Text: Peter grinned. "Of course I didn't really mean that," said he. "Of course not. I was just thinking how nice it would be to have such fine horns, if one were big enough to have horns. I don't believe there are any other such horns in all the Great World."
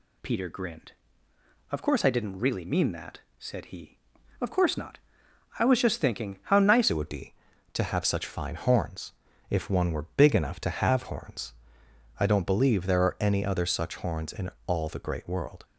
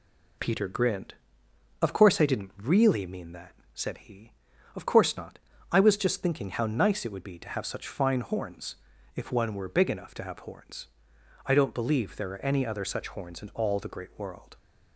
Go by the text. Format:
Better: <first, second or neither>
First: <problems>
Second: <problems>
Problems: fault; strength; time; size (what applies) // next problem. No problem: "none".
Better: second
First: changes voice at "it"; from 6.8 s on; 8.8 s long // pauses between "in" and "all"; slight; at 14.5 s; 0.16 s long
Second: none